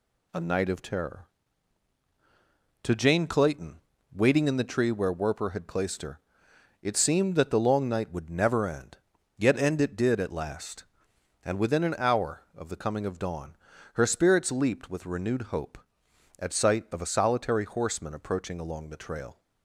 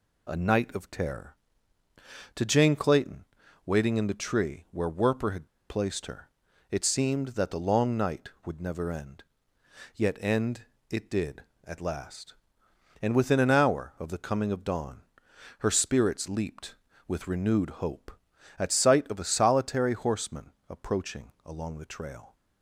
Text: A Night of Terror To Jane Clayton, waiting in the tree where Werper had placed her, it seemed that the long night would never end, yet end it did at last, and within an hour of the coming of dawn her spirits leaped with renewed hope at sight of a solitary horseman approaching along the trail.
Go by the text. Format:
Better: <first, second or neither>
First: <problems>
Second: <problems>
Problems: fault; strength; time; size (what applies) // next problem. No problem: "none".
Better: first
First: pauses between "dawn" and "her"; at 13.5 s; 0.38 s long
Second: pauses between "had" and "placed"; slight; at 5.4 s; 0.20 s long // pauses between "end" and "it"; slight; at 10.6 s; 0.28 s long // pauses between "dawn" and "her"; noticeable; at 15.0 s; 0.56 s long // pauses between "horseman" and "approaching"; slight; at 20.5 s; 0.18 s long